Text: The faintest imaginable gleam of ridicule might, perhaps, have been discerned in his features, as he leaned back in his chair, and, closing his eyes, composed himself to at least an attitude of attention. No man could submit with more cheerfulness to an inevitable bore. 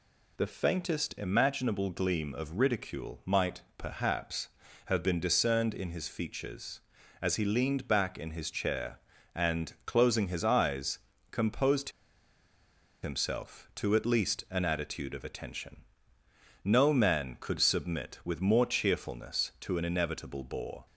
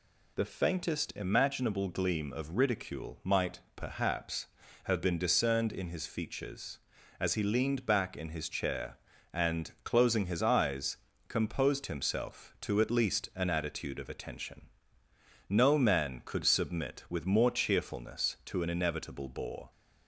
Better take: second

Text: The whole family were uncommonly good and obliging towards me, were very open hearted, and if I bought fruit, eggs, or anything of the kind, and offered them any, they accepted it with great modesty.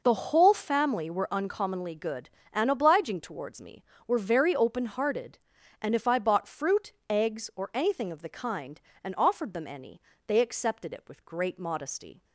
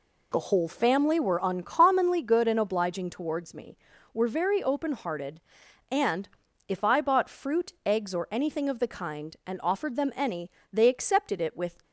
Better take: first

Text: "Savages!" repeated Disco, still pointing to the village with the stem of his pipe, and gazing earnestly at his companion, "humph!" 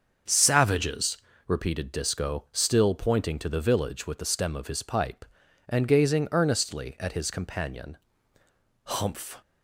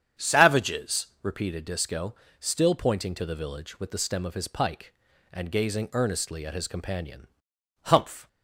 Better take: first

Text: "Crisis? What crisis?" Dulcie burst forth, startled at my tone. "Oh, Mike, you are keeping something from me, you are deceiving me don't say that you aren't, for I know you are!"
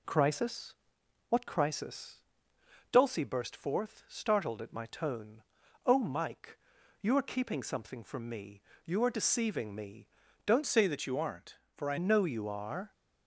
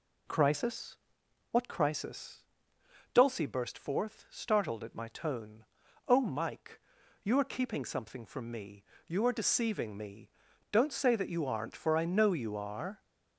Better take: second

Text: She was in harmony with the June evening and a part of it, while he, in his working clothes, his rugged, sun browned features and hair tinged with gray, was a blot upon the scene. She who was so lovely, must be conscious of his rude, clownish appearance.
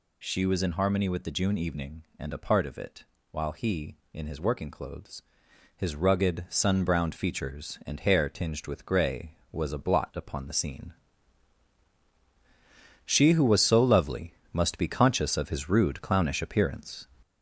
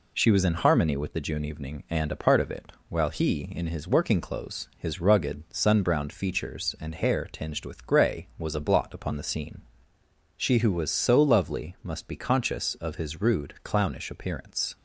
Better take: second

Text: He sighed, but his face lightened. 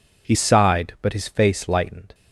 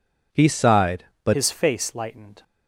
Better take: first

